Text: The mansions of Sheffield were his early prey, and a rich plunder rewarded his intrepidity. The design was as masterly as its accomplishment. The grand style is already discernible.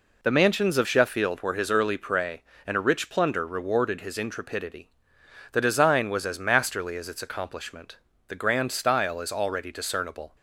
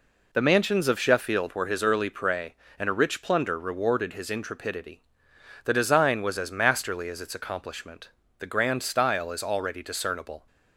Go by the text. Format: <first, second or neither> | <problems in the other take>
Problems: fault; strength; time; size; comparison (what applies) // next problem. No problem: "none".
neither | none